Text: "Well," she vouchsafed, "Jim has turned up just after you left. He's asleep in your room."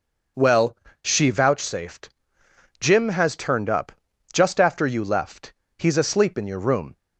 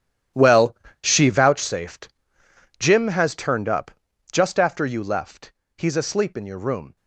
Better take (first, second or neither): first